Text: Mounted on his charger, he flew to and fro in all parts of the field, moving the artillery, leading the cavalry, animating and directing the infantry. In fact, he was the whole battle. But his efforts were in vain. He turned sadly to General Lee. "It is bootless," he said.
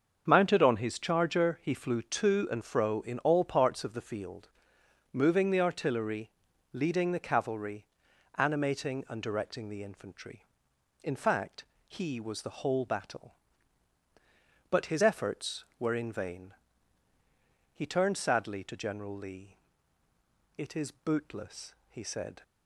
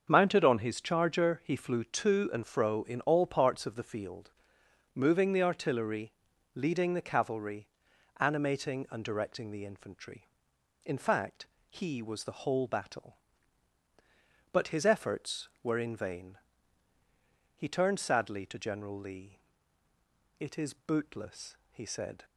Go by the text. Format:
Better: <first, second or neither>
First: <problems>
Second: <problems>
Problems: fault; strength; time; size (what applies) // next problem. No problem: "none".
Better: neither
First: starts louder than the rest; until 1.2 s; 7 dB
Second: starts louder than the rest; until 1.1 s; 7 dB